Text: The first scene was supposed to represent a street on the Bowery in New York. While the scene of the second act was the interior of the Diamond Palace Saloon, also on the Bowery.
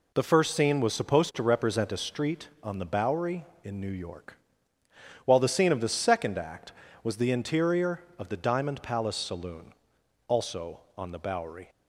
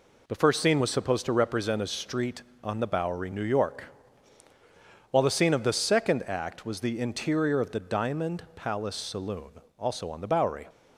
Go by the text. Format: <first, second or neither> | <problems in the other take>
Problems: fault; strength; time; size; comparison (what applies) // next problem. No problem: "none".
first | skips "in"; at 3.3 s